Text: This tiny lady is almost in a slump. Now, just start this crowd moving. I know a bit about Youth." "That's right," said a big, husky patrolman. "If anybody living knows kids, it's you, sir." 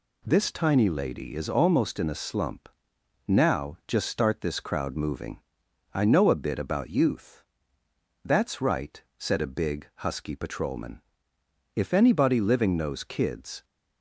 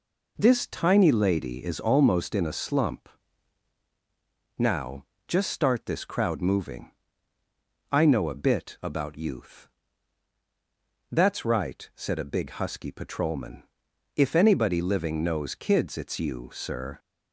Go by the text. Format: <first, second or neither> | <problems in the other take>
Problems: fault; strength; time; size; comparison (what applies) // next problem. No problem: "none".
second | stops before "it's you sir"; at 13.6 s